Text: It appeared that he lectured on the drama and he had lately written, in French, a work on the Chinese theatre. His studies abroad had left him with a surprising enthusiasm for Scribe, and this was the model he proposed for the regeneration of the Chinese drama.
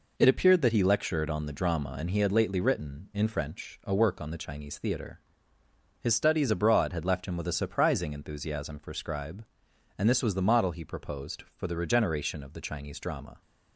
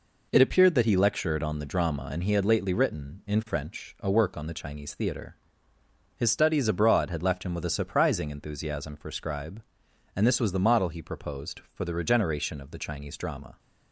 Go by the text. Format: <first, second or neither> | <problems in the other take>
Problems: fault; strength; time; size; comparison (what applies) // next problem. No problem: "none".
neither | none